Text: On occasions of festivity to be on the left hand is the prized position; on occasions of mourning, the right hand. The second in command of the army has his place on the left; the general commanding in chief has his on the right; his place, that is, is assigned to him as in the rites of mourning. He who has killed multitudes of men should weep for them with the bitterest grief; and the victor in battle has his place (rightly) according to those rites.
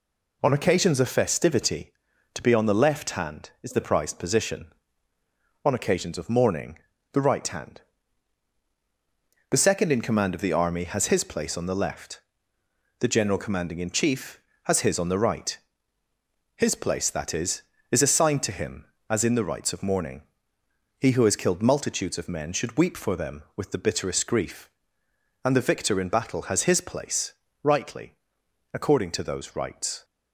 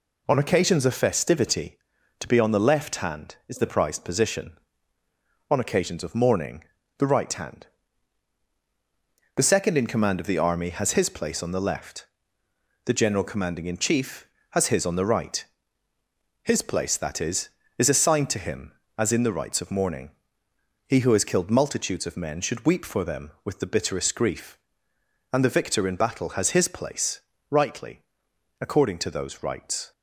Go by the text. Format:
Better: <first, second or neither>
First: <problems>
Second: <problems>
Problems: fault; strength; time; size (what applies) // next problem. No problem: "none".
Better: neither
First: none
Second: none